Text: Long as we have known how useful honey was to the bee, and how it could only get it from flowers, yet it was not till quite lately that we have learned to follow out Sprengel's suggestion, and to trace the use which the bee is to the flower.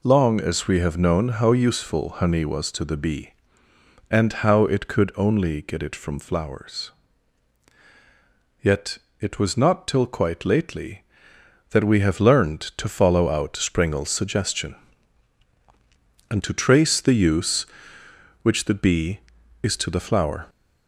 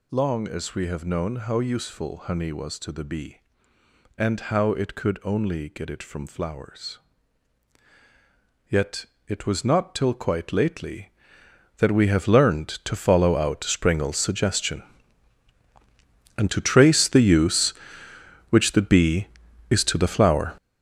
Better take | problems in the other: first | gets louder; strong; throughout; 10 dB // pauses between "yet" and "it"; slight; at 9.0 s; 0.24 s long; slight in the first

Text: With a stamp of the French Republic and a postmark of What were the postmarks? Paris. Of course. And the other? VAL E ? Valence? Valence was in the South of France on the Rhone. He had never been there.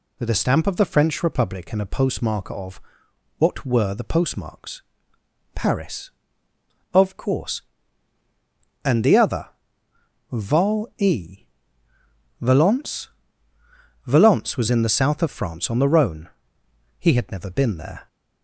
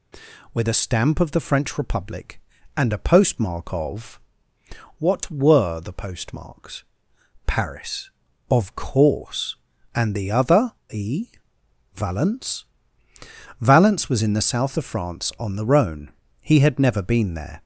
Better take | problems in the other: first | pauses between "of" and "What"; noticeable; at 4.2 s; 0.78 s long; noticeable in the first // skips "VAL"; at 10.8 s

